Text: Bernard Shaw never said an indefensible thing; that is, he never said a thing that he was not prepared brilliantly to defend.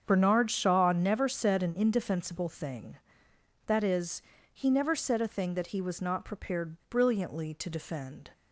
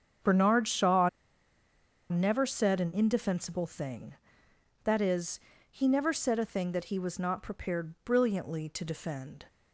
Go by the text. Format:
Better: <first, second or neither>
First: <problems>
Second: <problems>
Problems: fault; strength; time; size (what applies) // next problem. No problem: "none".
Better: first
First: starts louder than the rest; strong; until 1.0 s; 7.5 dB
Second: starts louder than the rest; strong; until 2.2 s; 7.5 dB // pauses between "Shaw" and "never"; at 1.0 s; 1.0 s long